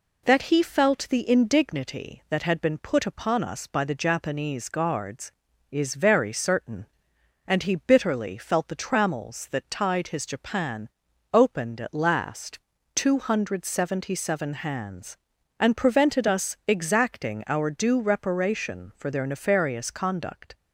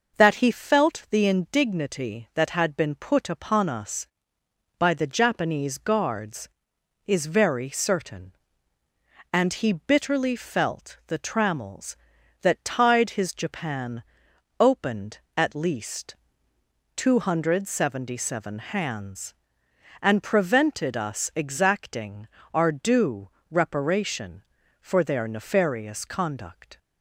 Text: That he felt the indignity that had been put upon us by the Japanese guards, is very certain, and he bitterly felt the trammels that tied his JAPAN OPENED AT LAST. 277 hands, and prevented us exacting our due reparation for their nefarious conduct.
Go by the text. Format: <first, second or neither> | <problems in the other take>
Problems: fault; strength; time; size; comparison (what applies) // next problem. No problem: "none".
first | pauses between "JAPAN" and "OPENED"; noticeable; at 14.0 s; 0.56 s long; noticeable in the first // says "Least" for "LAST"; at 15.5 s // pauses between "exacting" and "our"; slight; at 22.2 s; 0.26 s long // pauses between "due" and "reparation"; slight; at 23.2 s; 0.24 s long